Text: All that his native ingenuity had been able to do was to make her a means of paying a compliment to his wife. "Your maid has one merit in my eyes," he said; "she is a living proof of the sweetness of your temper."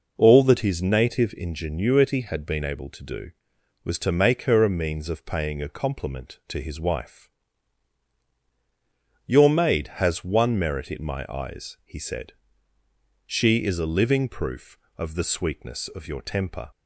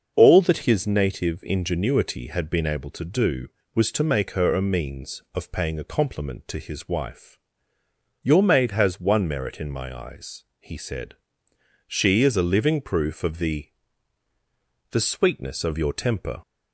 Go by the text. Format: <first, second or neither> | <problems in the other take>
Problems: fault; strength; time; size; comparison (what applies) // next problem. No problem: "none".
first | starts louder than the rest; until 1.1 s; 6 dB // says "the" twice; at 14.8 s